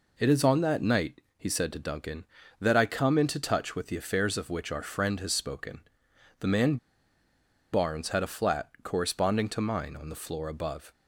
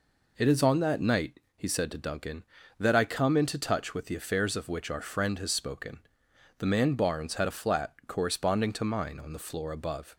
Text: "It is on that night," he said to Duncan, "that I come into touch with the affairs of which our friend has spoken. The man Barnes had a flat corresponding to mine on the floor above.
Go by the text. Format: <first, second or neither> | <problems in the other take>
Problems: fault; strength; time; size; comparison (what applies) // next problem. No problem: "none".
second | pauses between "man" and "Barnes"; noticeable; at 6.7 s; 0.96 s long